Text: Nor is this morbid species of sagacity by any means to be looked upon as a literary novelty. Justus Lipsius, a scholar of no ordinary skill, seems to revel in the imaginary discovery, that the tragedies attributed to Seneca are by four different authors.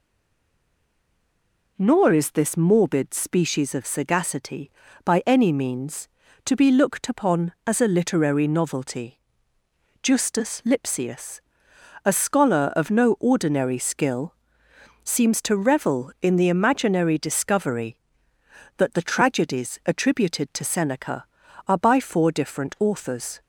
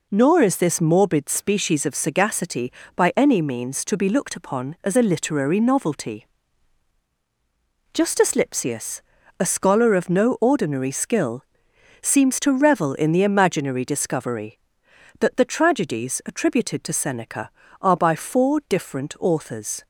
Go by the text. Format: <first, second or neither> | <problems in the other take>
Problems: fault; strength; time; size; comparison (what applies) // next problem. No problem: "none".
second | stays silent before the first word; noticeable; until 1.7 s; 1.7 s long